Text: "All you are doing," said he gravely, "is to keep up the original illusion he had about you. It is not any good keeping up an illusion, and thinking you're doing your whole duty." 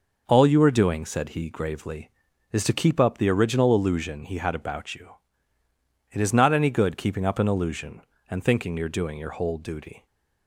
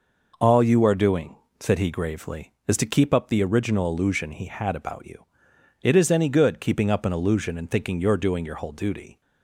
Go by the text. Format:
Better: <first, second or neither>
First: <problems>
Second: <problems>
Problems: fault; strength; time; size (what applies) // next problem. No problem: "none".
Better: first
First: none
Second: skips "not"; at 6.1 s